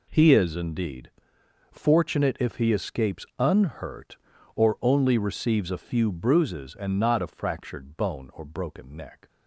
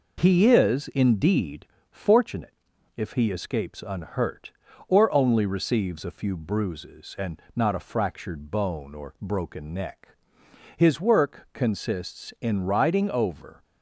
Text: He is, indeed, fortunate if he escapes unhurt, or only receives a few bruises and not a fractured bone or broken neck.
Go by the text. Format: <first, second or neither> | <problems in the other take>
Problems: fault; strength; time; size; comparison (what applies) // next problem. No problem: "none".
first | pauses between "fortunate" and "if"; at 2.5 s; 0.44 s long // goes on to say "His work consists in riding over"; strong; from 10.7 s on; 2.8 s long